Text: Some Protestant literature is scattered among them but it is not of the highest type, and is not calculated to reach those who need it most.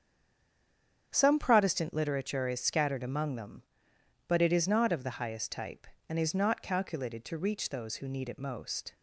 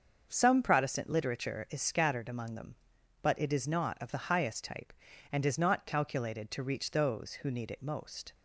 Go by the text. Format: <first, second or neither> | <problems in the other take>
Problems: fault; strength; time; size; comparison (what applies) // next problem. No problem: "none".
second | stays silent before the first word; until 1.1 s; 1.1 s long // starts louder than the rest; strong; until 2.1 s; 8 dB; also in the second